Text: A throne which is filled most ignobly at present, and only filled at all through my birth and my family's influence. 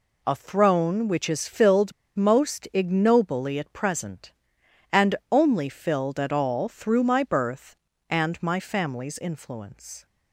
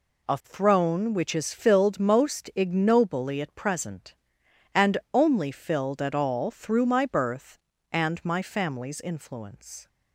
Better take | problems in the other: second | pauses between "filled" and "most"; slight; at 1.9 s; 0.24 s long // pauses between "and" and "only"; slight; at 5.1 s; 0.16 s long; slight in the second

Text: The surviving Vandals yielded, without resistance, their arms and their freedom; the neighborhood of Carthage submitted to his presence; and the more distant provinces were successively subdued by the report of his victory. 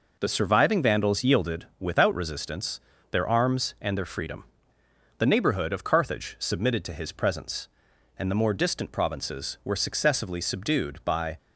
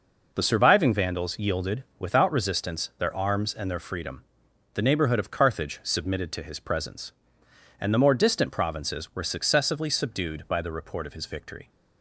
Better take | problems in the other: second | stops before "the report of his victory"; at 11.3 s

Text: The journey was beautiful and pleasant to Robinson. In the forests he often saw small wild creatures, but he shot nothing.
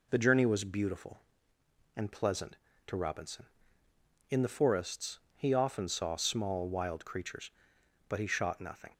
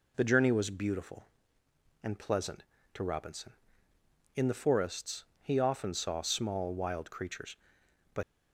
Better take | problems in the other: first | pauses between "forests" and "he"; slight; at 5.2 s; 0.16 s long; slight in the first // stops before "he shot nothing"; at 8.2 s

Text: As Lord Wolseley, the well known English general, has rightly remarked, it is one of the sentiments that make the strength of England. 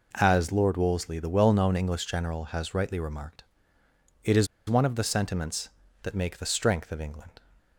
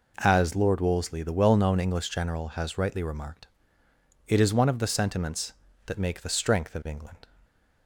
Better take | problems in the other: second | pauses between "is" and "one"; slight; at 4.4 s; 0.22 s long

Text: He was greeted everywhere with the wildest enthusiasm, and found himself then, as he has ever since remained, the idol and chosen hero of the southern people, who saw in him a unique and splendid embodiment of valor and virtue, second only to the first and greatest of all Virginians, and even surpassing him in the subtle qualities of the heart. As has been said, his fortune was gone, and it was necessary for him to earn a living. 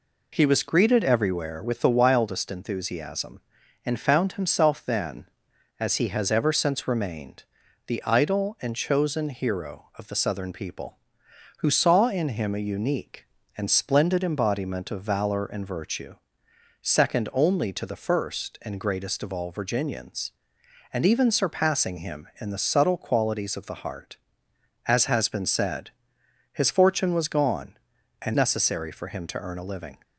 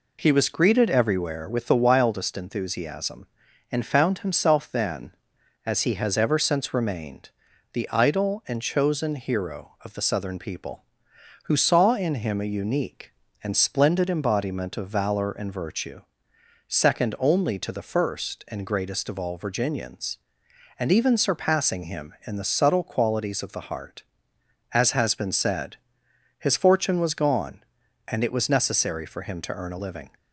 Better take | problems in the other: second | skips "it was"; at 28.3 s

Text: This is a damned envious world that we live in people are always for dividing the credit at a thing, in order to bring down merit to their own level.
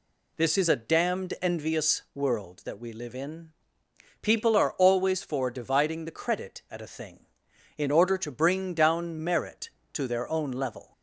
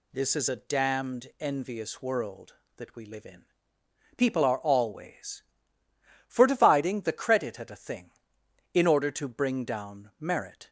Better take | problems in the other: first | pauses between "in" and "people"; noticeable; at 3.4 s; 0.72 s long; noticeable in the first // stops before "to their own level"; at 10.6 s

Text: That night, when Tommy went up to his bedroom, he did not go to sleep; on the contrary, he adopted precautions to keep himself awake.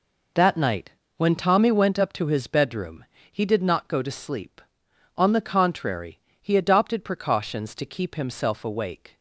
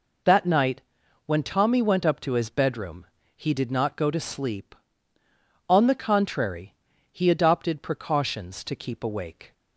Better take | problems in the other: first | skips "himself"; at 9.0 s

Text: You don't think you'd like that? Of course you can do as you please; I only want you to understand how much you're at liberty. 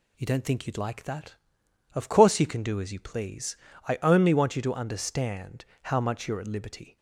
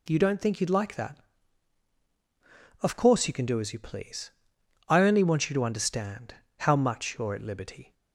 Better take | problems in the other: neither | pauses between "understand" and "how"; slight; the same in both

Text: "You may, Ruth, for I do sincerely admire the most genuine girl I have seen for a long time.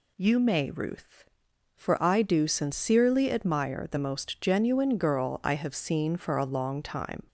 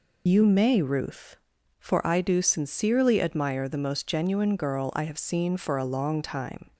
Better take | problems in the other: first | loses the start of "You"; at 0.2 s; 60 ms

